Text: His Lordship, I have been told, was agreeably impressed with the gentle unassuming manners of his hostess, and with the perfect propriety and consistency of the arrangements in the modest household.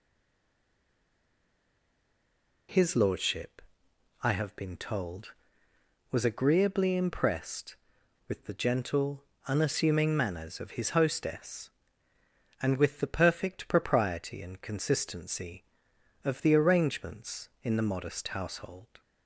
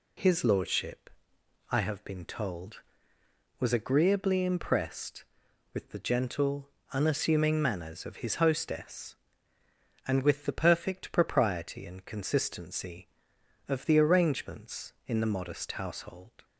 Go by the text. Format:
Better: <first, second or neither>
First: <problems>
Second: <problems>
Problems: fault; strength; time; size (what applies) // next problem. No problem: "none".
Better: second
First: stays silent before the first word; strong; until 2.6 s; 2.6 s long // pauses between "gentle" and "unassuming"; slight; at 9.2 s; 0.26 s long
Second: pauses between "gentle" and "unassuming"; slight; at 6.6 s; 0.26 s long